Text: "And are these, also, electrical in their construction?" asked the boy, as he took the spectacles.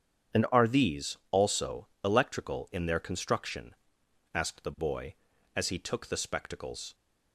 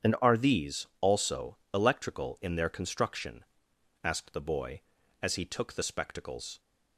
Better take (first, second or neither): neither